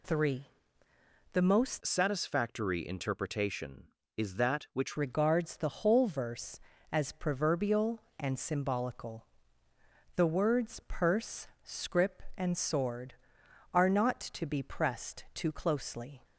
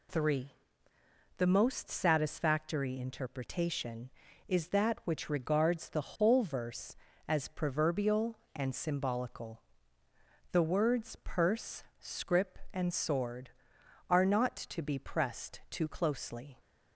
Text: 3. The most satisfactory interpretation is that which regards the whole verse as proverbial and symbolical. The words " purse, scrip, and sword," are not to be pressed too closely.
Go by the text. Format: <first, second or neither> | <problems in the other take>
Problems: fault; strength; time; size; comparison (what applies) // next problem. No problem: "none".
second | changes voice from "satisfactory" to "which"; from 1.8 to 4.9 s; 3.1 s long